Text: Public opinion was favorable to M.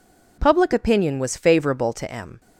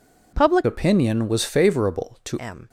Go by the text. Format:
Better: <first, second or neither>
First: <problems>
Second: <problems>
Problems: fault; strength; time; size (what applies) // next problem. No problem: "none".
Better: first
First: none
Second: changes voice from "opinion" to "to"; from 0.6 to 2.3 s; 1.7 s long